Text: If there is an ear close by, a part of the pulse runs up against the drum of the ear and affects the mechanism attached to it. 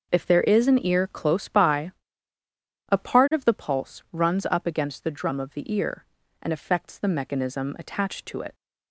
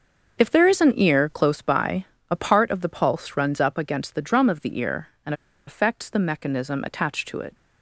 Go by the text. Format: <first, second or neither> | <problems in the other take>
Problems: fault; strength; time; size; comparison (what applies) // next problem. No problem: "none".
first | starts louder than the rest; until 1.4 s; 6.5 dB // pauses between "and" and "affects"; slight; at 5.3 s; 0.33 s long